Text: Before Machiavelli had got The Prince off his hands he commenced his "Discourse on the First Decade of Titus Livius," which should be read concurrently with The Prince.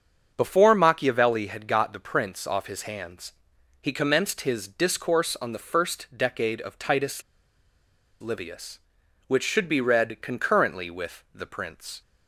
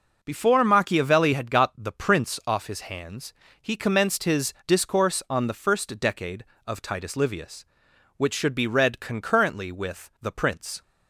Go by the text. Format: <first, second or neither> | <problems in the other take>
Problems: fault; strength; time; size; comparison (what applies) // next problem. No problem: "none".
second | starts louder than the rest; until 1.3 s; 7 dB // pauses between "hands" and "he"; noticeable; at 3.3 s; 0.50 s long; slight in the second // pauses between "Titus" and "Livius"; at 7.2 s; 0.99 s long